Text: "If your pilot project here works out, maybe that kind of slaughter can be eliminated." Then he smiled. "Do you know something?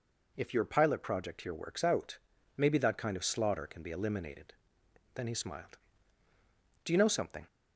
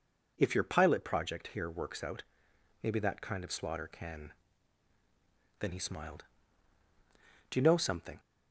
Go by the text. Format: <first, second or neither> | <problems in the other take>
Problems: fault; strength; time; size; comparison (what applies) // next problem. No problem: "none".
first | skips "be eliminated"; at 4.9 s